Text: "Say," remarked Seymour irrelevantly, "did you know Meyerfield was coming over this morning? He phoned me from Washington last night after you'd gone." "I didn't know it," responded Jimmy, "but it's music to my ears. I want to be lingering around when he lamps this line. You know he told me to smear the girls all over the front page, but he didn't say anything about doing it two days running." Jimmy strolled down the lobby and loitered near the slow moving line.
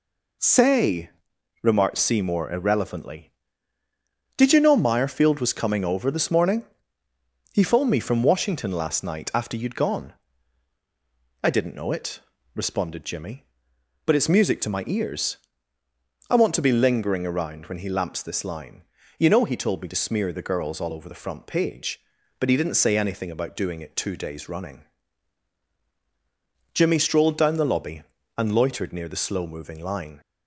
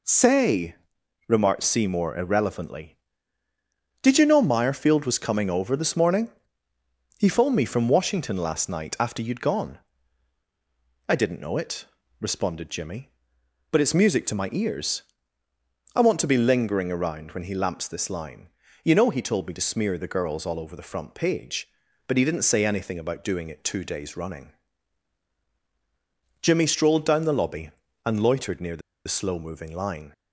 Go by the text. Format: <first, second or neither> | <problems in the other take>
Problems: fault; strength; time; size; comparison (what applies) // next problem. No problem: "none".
first | pauses between "the" and "slow"; slight; at 28.8 s; 0.27 s long